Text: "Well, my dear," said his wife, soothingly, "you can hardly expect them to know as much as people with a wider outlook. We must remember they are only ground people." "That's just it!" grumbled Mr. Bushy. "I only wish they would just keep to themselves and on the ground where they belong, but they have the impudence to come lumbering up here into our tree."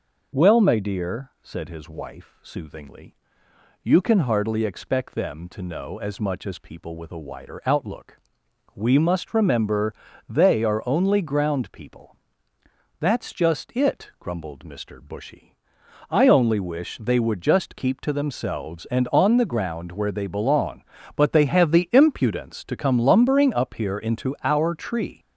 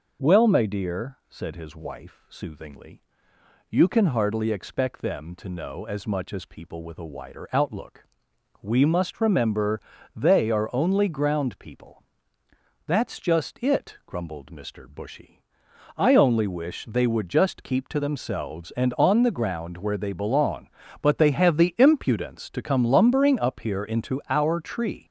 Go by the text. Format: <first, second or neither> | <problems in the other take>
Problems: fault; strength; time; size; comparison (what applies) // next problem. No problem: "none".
neither | pauses between "remember" and "they"; slight; the same in both